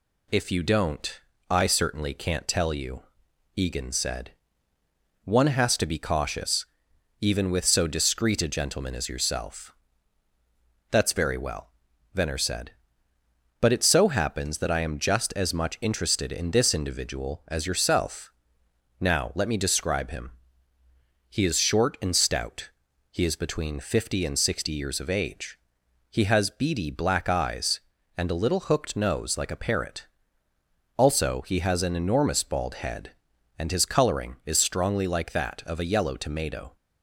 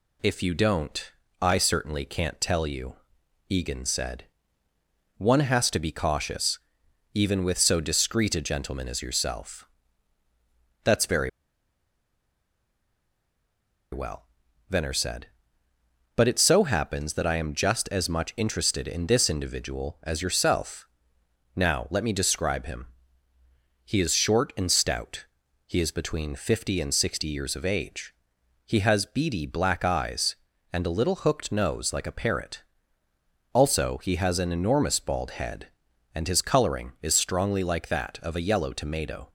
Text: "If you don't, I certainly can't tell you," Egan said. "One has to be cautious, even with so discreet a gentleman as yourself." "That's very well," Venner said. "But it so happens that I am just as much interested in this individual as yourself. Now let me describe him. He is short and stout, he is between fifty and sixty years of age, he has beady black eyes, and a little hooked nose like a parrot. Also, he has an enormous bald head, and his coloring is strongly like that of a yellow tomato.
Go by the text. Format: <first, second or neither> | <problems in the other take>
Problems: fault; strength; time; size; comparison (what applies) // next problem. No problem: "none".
first | pauses between "very" and "well"; strong; at 11.2 s; 2.6 s long